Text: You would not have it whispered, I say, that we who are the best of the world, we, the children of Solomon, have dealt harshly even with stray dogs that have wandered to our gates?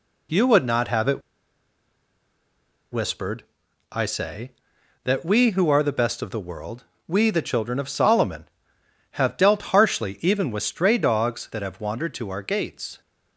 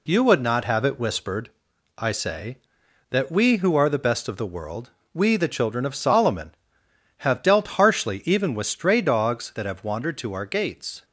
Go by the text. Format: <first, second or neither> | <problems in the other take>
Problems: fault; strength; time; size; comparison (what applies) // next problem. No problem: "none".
second | pauses between "it" and "whispered"; strong; at 1.2 s; 1.7 s long